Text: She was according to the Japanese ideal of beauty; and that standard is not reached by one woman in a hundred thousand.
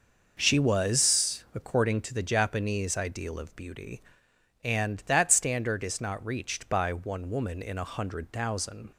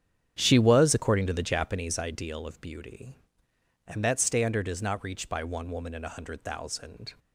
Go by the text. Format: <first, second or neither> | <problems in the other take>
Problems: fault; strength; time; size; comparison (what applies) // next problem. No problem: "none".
first | starts louder than the rest; strong; until 2.1 s; 9.5 dB